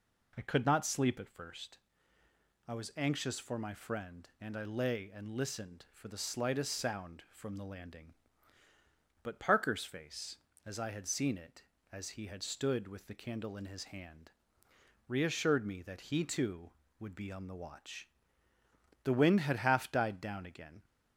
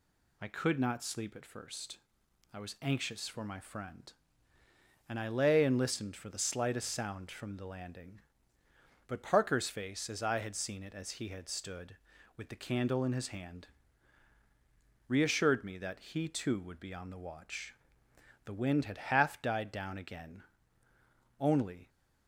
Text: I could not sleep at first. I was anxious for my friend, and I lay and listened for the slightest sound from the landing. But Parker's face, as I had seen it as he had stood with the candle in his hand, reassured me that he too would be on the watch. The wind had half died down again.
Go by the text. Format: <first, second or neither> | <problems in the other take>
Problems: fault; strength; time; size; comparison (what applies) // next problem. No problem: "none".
first | goes on to say "Only"; slight; from 21.4 s on; 0.48 s long